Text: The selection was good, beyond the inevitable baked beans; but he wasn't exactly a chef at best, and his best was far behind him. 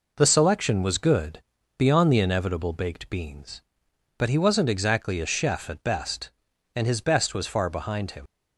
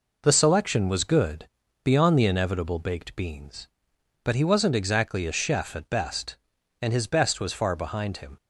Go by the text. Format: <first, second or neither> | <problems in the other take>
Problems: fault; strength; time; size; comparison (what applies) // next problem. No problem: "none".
second | leaves "him" unfinished; at 8.2 s; 45 ms